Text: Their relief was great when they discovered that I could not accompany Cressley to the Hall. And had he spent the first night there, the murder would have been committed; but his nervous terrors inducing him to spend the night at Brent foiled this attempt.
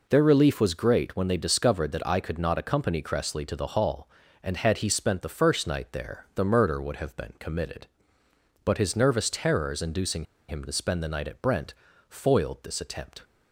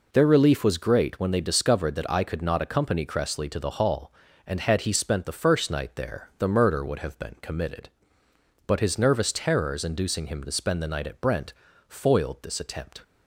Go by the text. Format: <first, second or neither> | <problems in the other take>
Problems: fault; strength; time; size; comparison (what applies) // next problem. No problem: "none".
second | pauses between "inducing" and "him"; slight; at 10.2 s; 0.23 s long // pauses between "Brent" and "foiled"; slight; at 11.7 s; 0.36 s long; slight in the second